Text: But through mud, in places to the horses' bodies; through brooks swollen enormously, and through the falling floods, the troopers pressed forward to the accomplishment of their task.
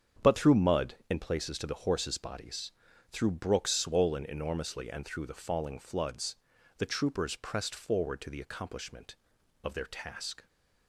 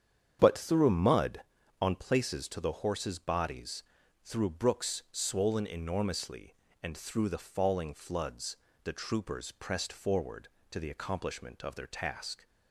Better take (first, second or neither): first